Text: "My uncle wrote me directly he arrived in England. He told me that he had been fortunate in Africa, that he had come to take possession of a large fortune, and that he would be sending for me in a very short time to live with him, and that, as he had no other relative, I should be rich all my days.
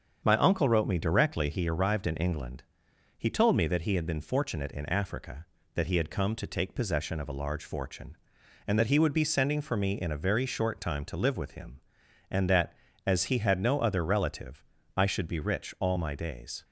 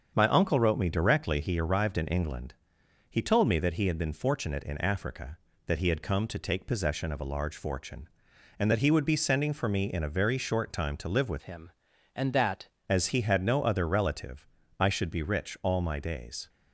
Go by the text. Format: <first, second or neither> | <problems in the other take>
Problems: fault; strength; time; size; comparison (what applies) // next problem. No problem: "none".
first | starts louder than the rest; strong; until 1.1 s; 7 dB; strong in the first // changes voice from "him" to "that"; from 11.4 to 12.6 s; 1.2 s long